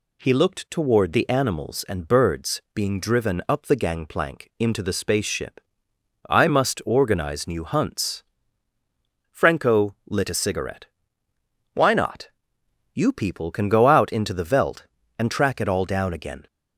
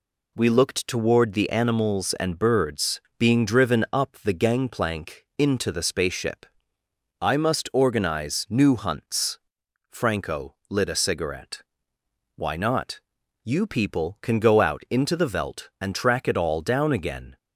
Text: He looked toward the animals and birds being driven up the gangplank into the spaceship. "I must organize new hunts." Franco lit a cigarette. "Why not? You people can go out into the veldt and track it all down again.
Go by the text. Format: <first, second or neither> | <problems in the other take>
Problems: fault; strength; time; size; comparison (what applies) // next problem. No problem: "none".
first | says "We" for "He"; at 0.3 s // pauses between "birds" and "being"; slight; at 3.0 s; 0.18 s long // pauses between "Franco" and "lit"; slight; at 10.5 s; 0.16 s long